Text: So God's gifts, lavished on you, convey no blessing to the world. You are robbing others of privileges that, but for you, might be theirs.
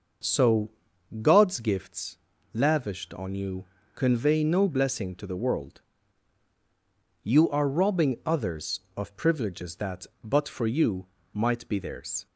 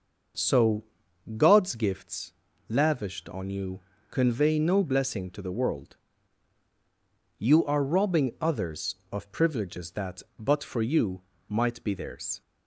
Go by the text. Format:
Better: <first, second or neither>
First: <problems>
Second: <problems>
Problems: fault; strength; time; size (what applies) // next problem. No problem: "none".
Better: neither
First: starts louder than the rest; until 1.7 s; 6.5 dB // pauses between "So" and "God's"; noticeable; at 0.7 s; 0.52 s long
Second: starts louder than the rest; until 1.9 s; 6.5 dB // pauses between "So" and "God's"; noticeable; at 0.8 s; 0.54 s long